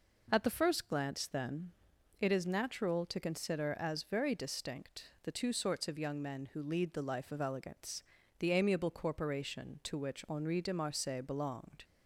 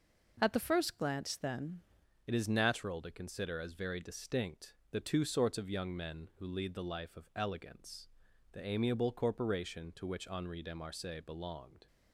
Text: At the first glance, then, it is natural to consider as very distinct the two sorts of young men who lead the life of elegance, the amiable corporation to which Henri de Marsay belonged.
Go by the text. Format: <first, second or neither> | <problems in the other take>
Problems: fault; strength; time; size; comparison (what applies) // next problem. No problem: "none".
first | changes voice at "it"; from 2.2 s on; 9.6 s long // pauses between "distinct" and "the"; slight; at 4.7 s; 0.16 s long